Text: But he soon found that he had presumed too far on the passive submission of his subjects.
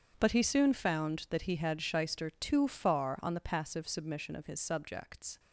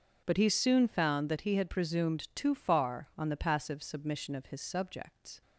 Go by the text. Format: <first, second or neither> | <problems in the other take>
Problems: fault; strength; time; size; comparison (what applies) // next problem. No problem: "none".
second | starts louder than the rest; strong; until 1.1 s; 7.5 dB; also in the second // says "shyster" for "presumed"; at 1.8 s